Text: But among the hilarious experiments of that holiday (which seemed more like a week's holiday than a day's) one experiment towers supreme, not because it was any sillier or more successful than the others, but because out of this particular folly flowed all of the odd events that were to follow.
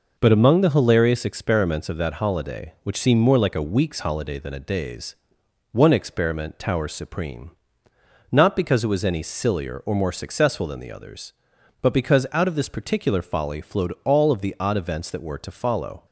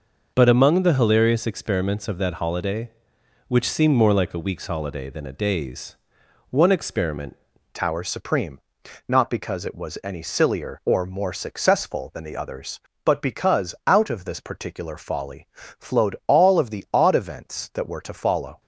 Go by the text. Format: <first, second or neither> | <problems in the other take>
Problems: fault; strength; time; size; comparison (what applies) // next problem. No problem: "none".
first | changes voice at "towers"; from 7.7 s on; 10.9 s long